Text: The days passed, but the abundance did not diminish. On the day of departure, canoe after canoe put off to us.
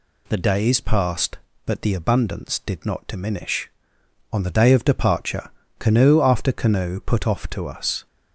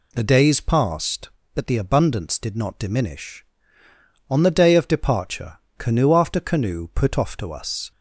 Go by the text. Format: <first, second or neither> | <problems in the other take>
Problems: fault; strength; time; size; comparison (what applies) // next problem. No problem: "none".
neither | none